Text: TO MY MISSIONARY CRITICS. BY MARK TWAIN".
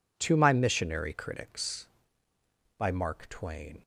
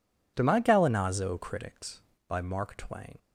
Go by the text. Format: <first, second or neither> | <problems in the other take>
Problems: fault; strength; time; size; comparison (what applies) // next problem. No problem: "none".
first | says "Gallinazo" for "MISSIONARY"; at 0.6 s